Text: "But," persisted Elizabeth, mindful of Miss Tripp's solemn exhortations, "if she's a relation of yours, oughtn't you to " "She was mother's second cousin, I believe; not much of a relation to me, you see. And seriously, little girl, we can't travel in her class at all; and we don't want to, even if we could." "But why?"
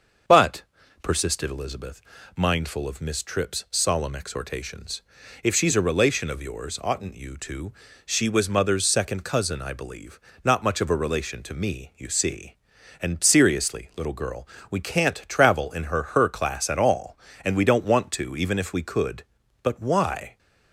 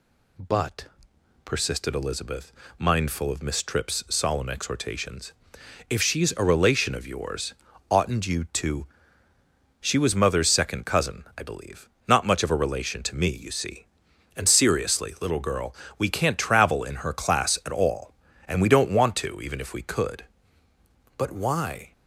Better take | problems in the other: second | starts louder than the rest; until 1.6 s; 6.5 dB // says "her" twice; at 16.0 s

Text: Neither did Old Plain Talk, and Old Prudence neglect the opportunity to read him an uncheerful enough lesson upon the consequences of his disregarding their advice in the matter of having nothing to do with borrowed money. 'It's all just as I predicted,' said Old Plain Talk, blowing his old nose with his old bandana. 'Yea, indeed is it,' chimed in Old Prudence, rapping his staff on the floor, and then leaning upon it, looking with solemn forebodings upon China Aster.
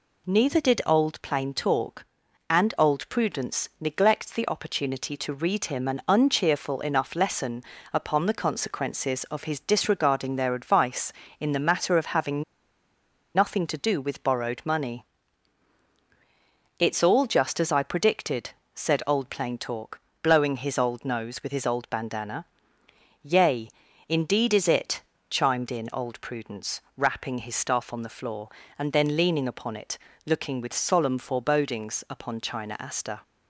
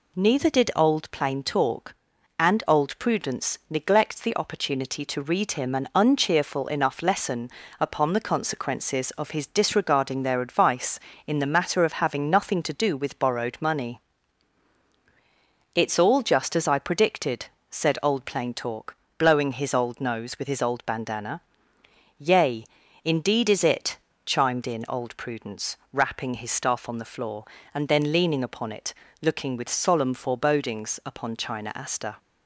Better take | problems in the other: second | pauses between "lesson" and "upon"; slight; at 7.6 s; 0.28 s long; slight in the second // pauses between "having" and "nothing"; noticeable; at 12.4 s; 0.91 s long

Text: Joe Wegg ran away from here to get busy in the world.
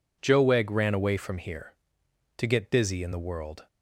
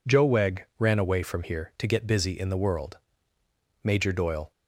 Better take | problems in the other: first | goes on to say "Major Doyle"; noticeable; from 3.8 s on; 0.68 s long

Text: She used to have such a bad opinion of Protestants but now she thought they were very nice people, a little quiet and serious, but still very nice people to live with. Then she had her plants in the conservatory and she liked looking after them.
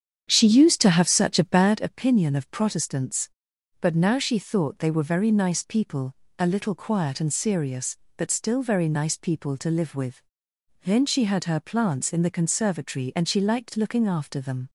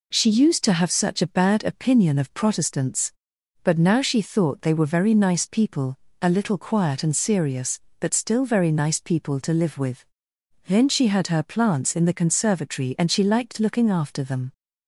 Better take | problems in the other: second | starts louder than the rest; strong; until 1.8 s; 8 dB

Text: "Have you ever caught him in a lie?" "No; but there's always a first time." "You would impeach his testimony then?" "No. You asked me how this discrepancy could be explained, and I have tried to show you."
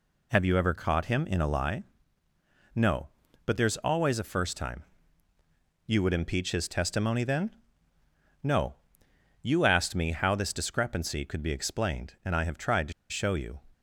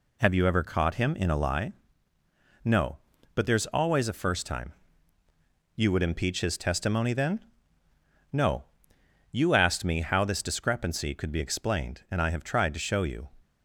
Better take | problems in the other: second | pauses between "to" and "show"; slight; at 12.9 s; 0.17 s long

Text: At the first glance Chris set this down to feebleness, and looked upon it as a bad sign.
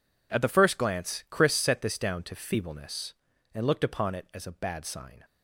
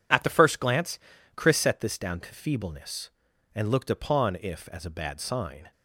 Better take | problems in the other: first | pauses between "glance" and "Chris"; at 0.9 s; 0.38 s long // says "if" for "it"; at 4.3 s

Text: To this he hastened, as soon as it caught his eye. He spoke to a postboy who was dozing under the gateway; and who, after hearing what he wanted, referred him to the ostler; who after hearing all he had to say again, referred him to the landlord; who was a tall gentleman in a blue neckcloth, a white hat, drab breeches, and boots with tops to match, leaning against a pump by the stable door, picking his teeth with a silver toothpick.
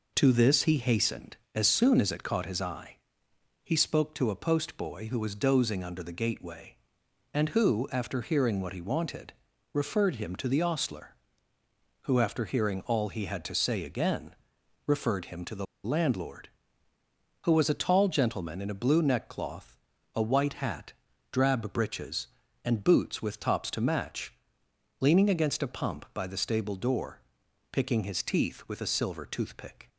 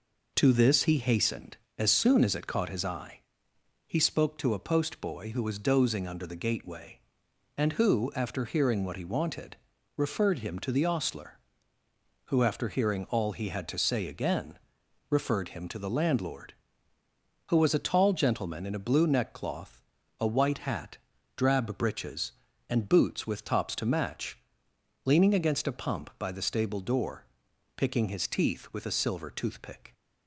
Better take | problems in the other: second | pauses between "the" and "landlord"; slight; at 15.6 s; 0.18 s long

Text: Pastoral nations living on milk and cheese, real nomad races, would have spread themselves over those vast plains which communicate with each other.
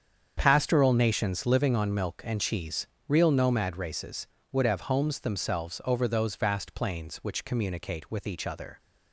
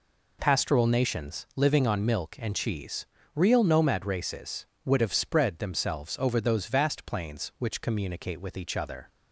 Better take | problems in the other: second | starts louder than the rest; strong; until 1.3 s; 7.5 dB // says "homes" for "spread"; at 4.8 s

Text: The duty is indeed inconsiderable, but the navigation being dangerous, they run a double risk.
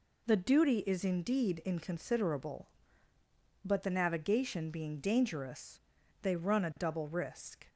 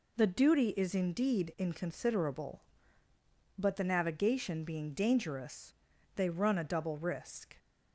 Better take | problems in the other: neither | none

